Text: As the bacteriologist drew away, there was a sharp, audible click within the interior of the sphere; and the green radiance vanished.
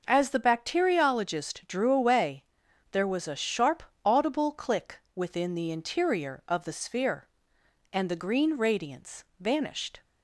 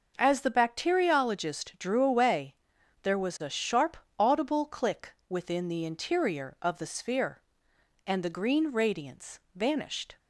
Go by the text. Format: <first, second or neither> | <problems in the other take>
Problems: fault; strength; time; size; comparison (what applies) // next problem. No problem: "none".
neither | pauses between "click" and "within"; slight; the same in both // pauses between "radiance" and "vanished"; slight; the same in both